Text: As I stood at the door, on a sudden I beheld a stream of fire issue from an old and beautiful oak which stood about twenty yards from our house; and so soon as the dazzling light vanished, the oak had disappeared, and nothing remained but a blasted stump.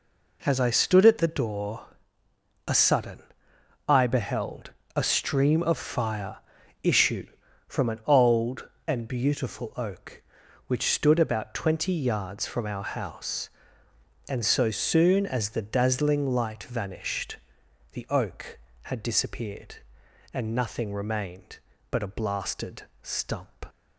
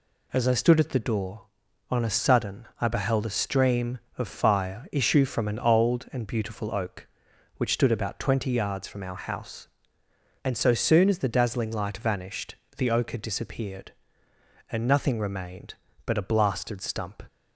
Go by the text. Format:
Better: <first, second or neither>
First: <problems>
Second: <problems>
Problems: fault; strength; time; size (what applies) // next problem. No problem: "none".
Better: second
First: skips "on"; at 2.2 s // pauses between "sudden" and "I"; noticeable; at 3.1 s; 0.68 s long // pauses between "beheld" and "a"; slight; at 4.7 s; 0.24 s long // pauses between "fire" and "issue"; noticeable; at 6.3 s; 0.46 s long // pauses between "blasted" and "stump"; slight; at 22.8 s; 0.18 s long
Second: none